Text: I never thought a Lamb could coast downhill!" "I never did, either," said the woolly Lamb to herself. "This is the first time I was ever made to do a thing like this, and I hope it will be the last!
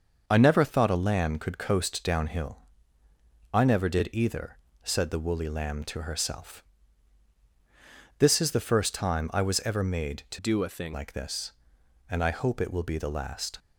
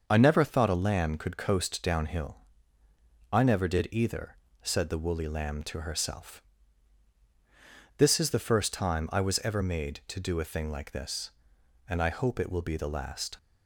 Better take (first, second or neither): second